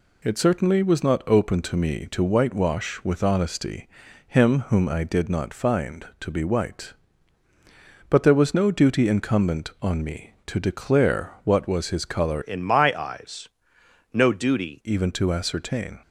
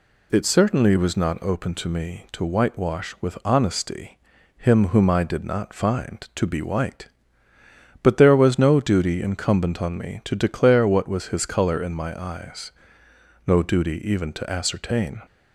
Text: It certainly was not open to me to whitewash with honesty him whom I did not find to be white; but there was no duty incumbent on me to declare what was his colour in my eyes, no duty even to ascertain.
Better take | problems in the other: second | pauses between "honesty" and "him"; at 3.8 s; 0.40 s long; also in the second // changes voice from "in" to "duty"; from 12.4 to 14.8 s; 2.4 s long

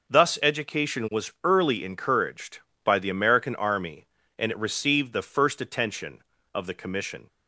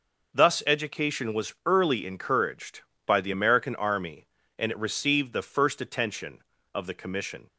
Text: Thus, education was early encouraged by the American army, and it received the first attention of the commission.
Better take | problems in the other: neither | none

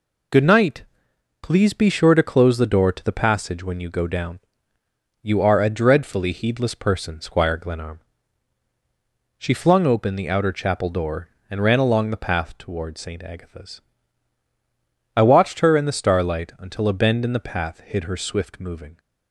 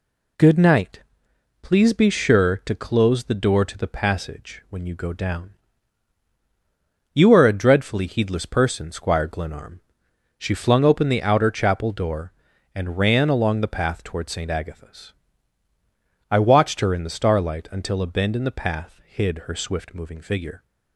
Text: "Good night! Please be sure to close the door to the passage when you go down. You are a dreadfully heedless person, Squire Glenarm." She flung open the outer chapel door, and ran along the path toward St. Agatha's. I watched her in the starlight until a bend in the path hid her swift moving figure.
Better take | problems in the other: second | stops before "figure"; at 18.9 s

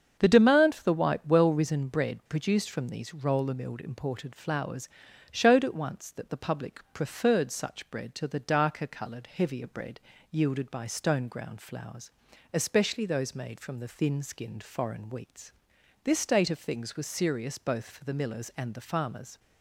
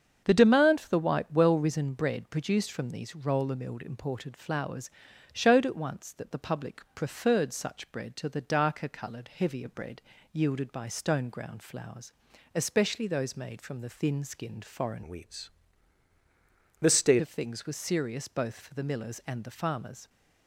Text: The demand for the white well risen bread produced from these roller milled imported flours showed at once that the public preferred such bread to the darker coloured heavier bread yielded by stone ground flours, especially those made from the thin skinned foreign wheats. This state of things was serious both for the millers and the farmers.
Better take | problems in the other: first | starts louder than the rest; strong; until 1.2 s; 7 dB; strong in the first // pauses between "flours" and "showed"; at 4.8 s; 0.44 s long; also in the first // pauses between "bread" and "yielded"; slight; at 10.0 s; 0.30 s long; slight in the first // changes voice from "wheats" to "state"; from 15.0 to 17.2 s; 2.2 s long

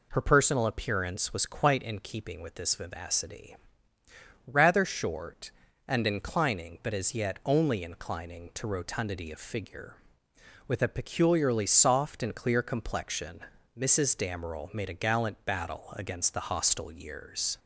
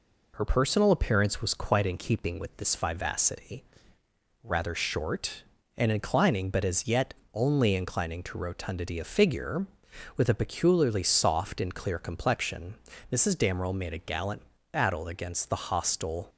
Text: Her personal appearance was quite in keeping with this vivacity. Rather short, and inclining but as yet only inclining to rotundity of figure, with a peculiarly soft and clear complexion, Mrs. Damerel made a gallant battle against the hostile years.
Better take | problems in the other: first | pauses between "yet" and "only"; slight; at 7.1 s; 0.20 s long // pauses between "gallant" and "battle"; slight; at 14.4 s; 0.30 s long // stops before "years"; at 16.2 s

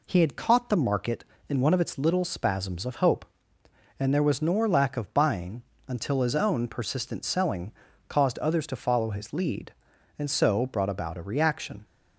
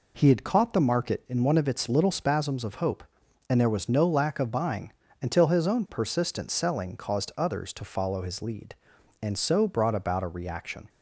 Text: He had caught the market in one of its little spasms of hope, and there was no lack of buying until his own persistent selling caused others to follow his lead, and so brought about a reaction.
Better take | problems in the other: second | says "nor" for "no"; at 4.4 s // pauses between "buying" and "until"; slight; at 5.6 s; 0.24 s long; slight in the second // pauses between "selling" and "caused"; at 7.7 s; 0.38 s long

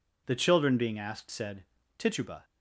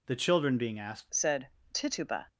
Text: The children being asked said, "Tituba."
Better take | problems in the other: first | changes voice at "said"; from 1.0 s on; 1.2 s long

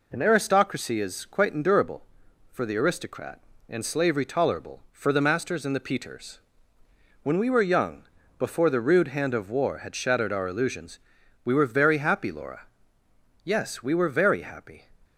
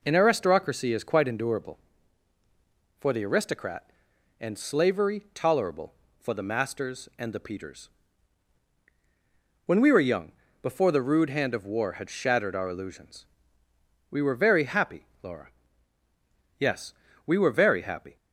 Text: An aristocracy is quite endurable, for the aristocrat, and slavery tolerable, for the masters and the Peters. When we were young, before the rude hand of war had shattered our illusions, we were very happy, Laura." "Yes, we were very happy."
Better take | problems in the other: neither | none

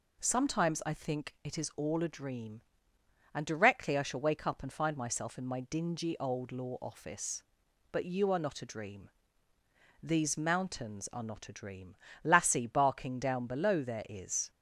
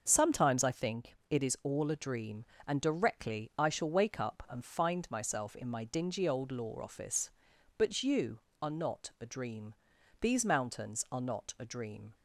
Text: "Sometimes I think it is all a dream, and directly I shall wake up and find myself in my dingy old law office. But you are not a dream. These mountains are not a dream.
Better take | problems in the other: second | goes on to say "Lassie barking down below there is"; strong; from 12.2 s on; 2.2 s long

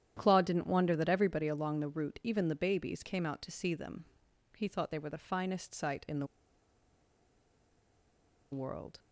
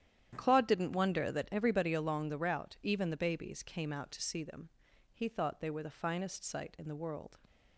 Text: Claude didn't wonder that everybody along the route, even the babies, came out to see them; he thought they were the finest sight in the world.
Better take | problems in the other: second | starts louder than the rest; strong; until 1.1 s; 10 dB; strong in the second // pauses between "the" and "world"; strong; at 6.2 s; 2.2 s long

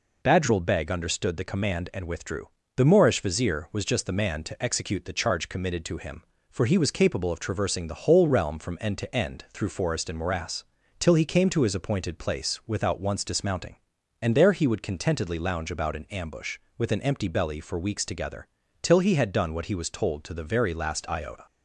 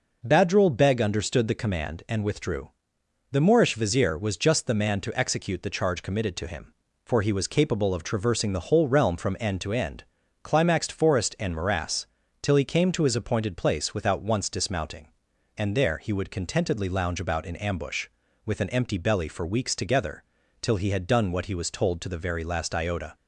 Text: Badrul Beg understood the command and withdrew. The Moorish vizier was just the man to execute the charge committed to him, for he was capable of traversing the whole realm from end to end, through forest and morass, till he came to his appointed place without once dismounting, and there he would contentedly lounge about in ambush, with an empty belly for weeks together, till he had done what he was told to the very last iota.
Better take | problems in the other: first | says "climaxed" for "through"; at 10.4 s

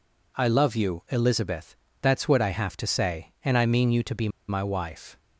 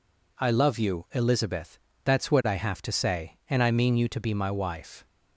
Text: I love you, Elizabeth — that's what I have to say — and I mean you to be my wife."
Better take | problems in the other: second | pauses between "be" and "my"; slight; at 4.2 s; 0.19 s long

